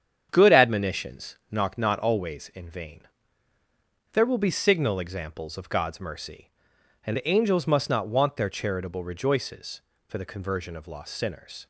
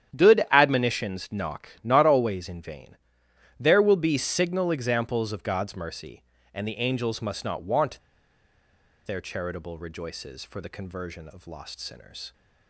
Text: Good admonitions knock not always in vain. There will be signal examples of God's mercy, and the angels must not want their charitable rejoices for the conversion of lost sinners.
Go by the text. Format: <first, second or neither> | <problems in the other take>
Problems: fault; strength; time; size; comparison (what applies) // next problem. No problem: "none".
first | starts louder than the rest; strong; until 1.2 s; 10 dB; strong in the first // pauses between "knock" and "not"; slight; at 1.6 s; 0.16 s long // pauses between "want" and "their"; at 7.9 s; 1.0 s long